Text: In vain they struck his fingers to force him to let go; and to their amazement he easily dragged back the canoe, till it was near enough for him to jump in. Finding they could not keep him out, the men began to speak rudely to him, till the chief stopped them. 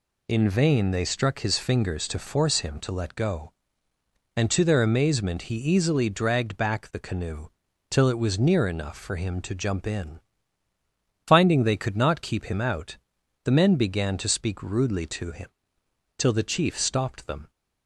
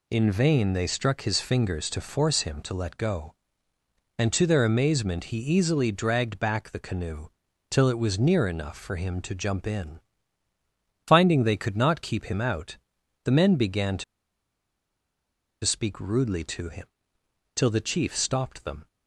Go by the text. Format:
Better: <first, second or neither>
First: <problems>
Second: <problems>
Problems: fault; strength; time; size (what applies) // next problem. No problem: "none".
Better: first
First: none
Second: pauses between "to" and "speak"; strong; at 14.0 s; 1.6 s long